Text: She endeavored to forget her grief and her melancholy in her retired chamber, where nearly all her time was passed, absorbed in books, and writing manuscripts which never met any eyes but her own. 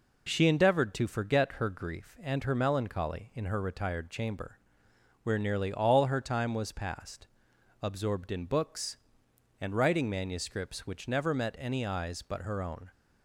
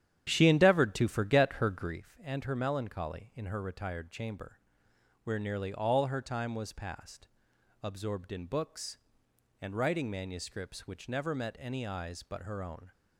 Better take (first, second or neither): first